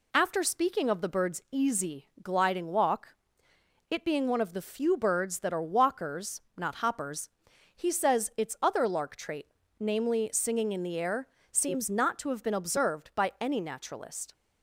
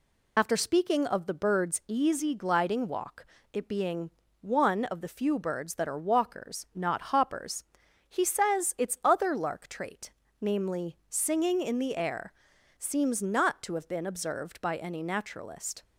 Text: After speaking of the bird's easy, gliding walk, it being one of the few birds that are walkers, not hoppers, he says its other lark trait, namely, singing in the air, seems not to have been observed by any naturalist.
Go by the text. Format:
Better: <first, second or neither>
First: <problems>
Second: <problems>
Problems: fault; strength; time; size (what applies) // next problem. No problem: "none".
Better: first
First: none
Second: loses the start of "After"; at 0.3 s; 45 ms // pauses between "being" and "one"; slight; at 4.1 s; 0.28 s long